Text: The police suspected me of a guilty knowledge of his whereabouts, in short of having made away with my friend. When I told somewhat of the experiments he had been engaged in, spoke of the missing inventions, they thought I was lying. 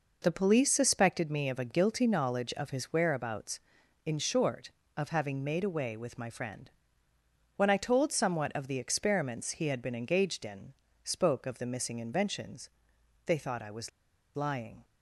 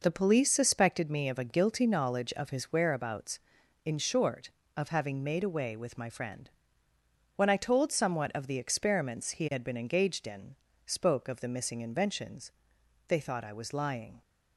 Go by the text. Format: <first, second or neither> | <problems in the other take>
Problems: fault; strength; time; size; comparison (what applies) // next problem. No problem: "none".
second | pauses between "was" and "lying"; noticeable; at 13.8 s; 0.46 s long